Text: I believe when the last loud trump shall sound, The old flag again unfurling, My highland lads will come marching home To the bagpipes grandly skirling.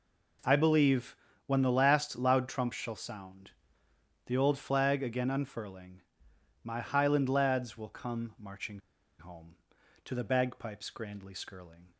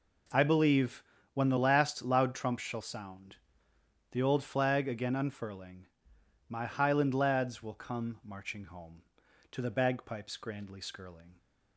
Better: second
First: pauses between "believe" and "when"; slight; at 1.1 s; 0.30 s long // pauses between "marching" and "home"; at 8.8 s; 0.39 s long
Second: pauses between "believe" and "when"; slight; at 1.0 s; 0.30 s long

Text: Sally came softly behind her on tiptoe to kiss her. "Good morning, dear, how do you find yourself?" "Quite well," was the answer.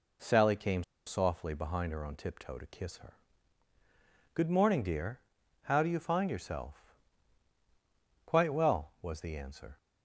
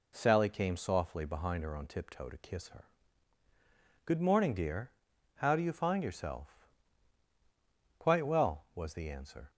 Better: second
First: pauses between "came" and "softly"; slight; at 0.8 s; 0.23 s long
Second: none

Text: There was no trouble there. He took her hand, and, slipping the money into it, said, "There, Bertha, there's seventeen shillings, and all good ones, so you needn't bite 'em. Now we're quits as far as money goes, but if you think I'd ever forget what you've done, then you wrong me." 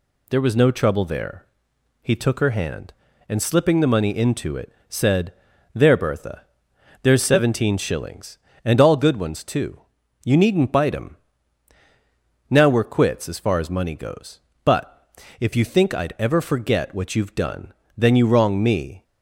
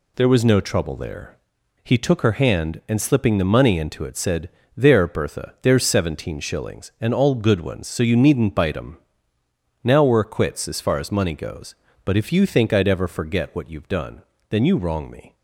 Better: second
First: says "too" for "so"; at 9.4 s // pauses between "but" and "if"; slight; at 15.0 s; 0.32 s long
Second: none

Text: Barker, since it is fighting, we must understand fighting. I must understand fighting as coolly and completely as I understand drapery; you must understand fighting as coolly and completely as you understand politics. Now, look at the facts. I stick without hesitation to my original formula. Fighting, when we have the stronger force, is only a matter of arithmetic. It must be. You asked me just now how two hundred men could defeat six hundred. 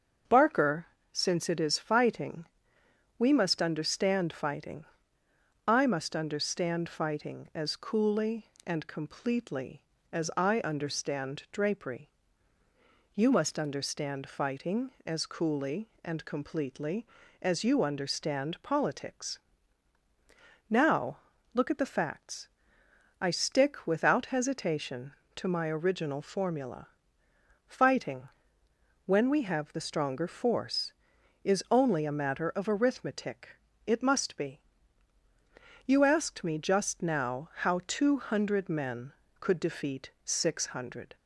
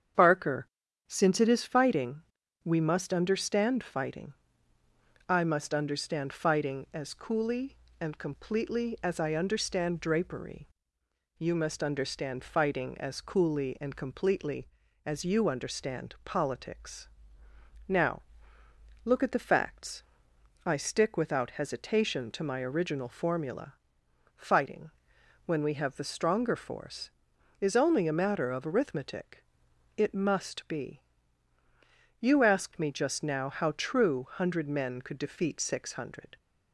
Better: first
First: starts louder than the rest; until 1.5 s; 7 dB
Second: starts louder than the rest; strong; until 1.5 s; 8 dB // says "true" for "two"; at 33.7 s

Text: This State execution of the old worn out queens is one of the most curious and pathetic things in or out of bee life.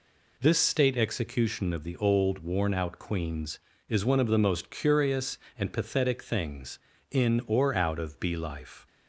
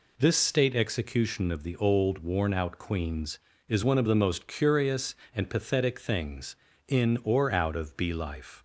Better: neither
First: none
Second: none

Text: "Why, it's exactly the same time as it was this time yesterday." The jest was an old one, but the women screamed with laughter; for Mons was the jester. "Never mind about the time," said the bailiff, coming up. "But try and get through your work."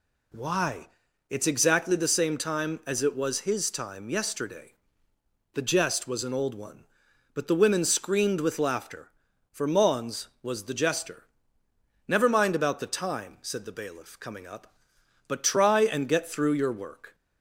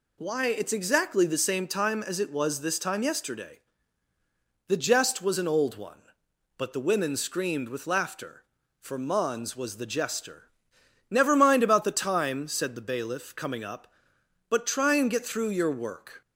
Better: second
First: says "his" for "this"; at 3.4 s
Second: none

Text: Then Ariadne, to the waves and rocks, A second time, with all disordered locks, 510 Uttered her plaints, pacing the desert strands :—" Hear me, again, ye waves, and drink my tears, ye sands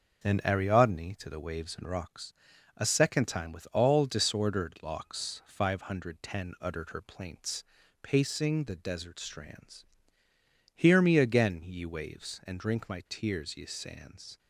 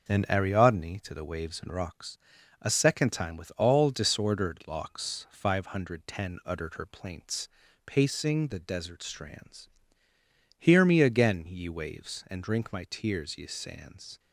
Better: neither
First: starts louder than the rest; until 1.3 s; 6.5 dB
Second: starts louder than the rest; until 1.1 s; 6 dB

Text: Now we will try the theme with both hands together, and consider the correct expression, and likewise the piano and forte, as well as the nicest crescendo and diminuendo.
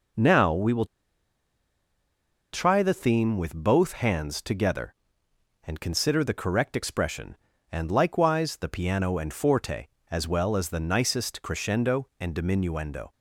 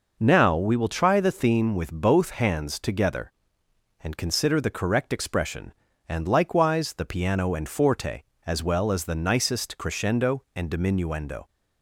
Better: second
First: pauses between "will" and "try"; strong; at 0.8 s; 1.6 s long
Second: none

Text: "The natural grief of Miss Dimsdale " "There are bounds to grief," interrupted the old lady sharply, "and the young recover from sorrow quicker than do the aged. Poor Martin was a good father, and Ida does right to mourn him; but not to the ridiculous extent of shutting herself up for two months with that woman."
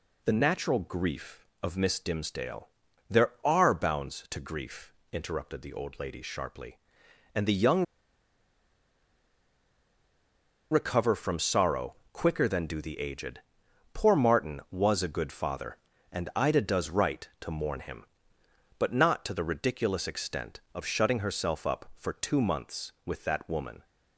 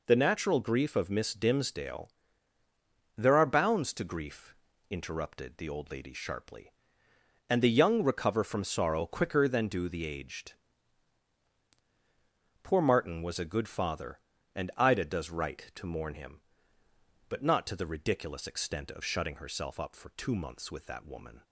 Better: second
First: pauses between "young" and "recover"; strong; at 7.8 s; 2.8 s long // pauses between "sorrow" and "quicker"; slight; at 11.9 s; 0.16 s long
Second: none

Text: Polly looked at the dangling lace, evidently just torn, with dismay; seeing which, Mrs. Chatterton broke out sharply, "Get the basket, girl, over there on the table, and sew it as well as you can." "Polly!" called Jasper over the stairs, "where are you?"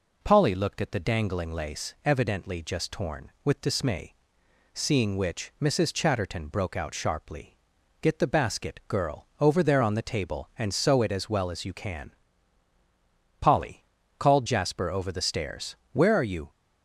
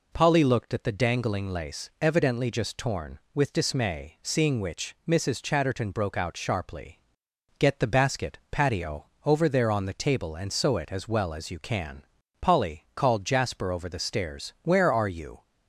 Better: first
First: none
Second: says "patio" for "girl"; at 8.4 s

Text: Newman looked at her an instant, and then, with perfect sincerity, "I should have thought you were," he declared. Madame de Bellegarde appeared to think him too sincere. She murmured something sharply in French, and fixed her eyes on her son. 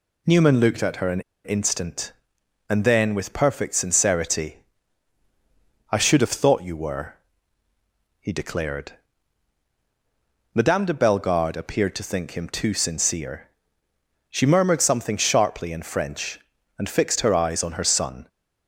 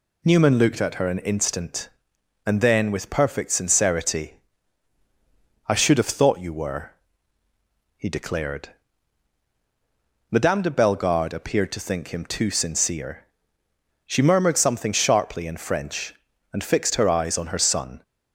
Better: second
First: pauses between "an" and "instant"; slight; at 1.1 s; 0.24 s long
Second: none

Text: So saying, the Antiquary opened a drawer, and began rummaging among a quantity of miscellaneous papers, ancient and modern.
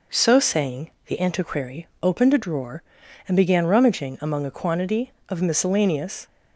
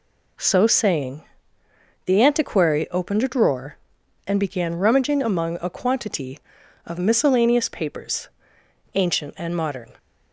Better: second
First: pauses between "Antiquary" and "opened"; slight; at 1.8 s; 0.16 s long // stops before "papers ancient and modern"; at 6.2 s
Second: none

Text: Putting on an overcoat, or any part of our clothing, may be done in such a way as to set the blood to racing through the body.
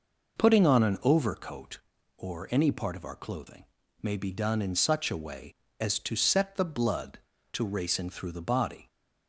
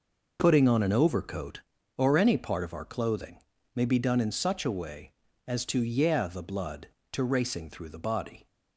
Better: first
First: none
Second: says "yeah" for "set"; at 5.8 s

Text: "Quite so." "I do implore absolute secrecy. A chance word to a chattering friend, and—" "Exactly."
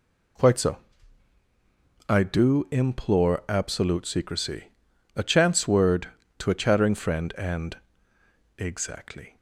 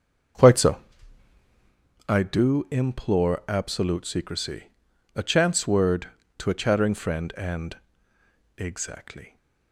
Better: first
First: none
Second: starts louder than the rest; until 1.8 s; 6.5 dB

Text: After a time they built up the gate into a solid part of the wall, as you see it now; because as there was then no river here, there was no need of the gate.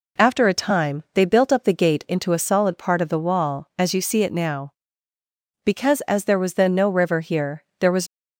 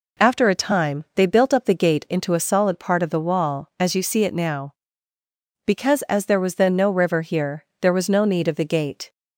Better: second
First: stops before "no need of the gate"; at 8.0 s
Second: none

